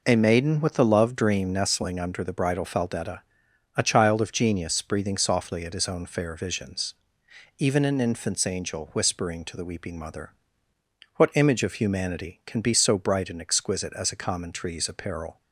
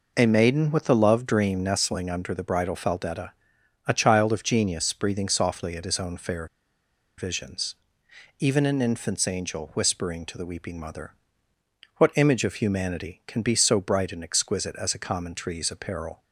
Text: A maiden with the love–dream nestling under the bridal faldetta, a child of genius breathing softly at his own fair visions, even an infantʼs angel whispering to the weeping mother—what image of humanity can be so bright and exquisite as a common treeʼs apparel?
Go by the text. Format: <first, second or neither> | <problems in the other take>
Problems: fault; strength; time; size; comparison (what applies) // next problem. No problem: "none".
first | pauses between "fair" and "visions"; noticeable; at 6.4 s; 0.72 s long